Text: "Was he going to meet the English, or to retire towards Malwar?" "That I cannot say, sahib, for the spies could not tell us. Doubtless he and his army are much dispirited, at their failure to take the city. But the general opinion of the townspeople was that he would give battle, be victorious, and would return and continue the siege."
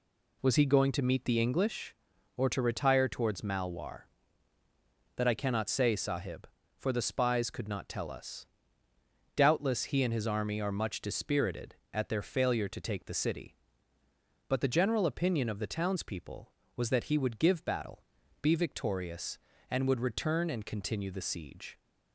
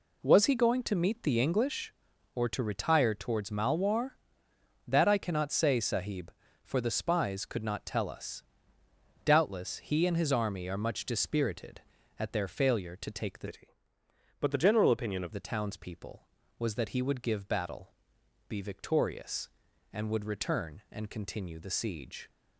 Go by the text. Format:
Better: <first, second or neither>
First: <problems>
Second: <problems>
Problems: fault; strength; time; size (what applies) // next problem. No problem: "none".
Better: first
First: none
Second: changes voice from "city" to "of"; from 13.4 to 15.3 s; 1.9 s long